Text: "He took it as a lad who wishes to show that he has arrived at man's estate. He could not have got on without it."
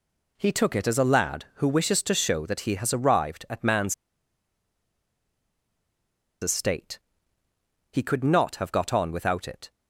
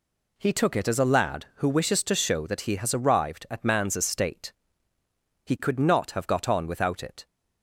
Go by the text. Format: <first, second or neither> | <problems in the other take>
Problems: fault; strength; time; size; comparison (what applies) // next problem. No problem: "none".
second | pauses between "man's" and "estate"; strong; at 3.9 s; 2.4 s long